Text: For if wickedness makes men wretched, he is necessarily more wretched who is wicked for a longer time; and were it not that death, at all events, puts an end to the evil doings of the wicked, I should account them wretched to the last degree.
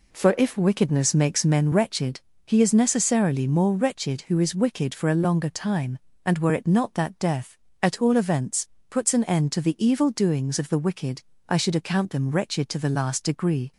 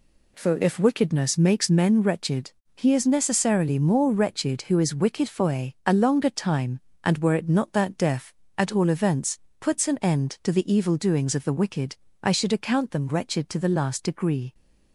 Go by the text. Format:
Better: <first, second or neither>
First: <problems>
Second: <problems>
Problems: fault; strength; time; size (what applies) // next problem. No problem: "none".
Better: first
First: none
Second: says "a" twice; at 5.8 s